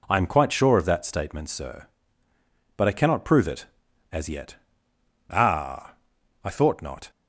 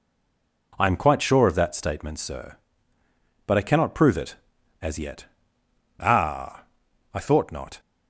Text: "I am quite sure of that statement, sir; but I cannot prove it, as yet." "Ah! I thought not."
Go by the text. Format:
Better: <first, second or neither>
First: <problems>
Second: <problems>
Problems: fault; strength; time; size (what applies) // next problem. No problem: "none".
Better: first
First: none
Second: stays silent before the first word; slight; until 0.7 s; 0.7 s long